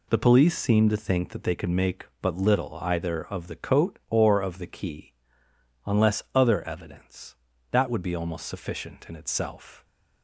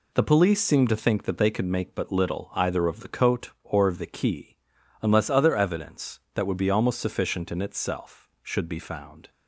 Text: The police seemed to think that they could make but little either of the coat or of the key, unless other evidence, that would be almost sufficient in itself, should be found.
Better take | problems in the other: second | stops before "should be found"; at 9.8 s

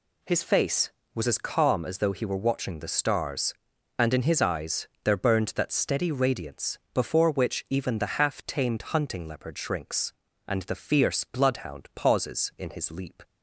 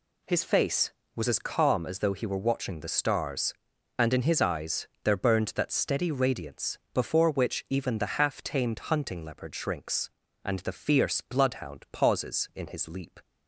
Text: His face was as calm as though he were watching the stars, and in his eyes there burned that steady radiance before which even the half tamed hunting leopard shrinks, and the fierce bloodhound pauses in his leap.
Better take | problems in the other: neither | pauses between "eyes" and "there"; slight; the same in both // pauses between "radiance" and "before"; slight; the same in both

